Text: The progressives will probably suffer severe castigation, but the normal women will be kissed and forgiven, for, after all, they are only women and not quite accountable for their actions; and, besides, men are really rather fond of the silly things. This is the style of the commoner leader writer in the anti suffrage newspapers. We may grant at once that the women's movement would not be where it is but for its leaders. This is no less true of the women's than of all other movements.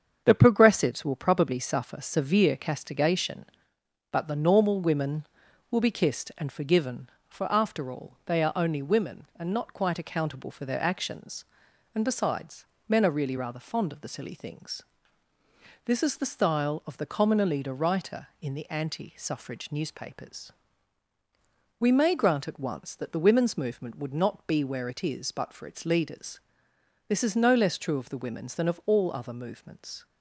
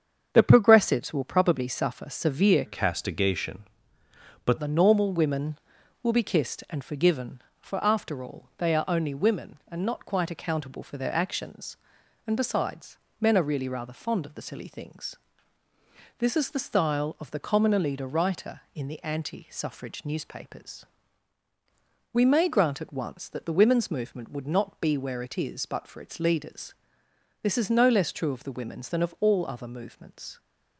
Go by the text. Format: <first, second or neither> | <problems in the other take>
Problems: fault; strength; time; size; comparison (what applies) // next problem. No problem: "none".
first | starts louder than the rest; strong; until 1.3 s; 7.5 dB; strong in the first // changes voice from "castigation" to "but"; from 2.6 to 4.5 s; 1.9 s long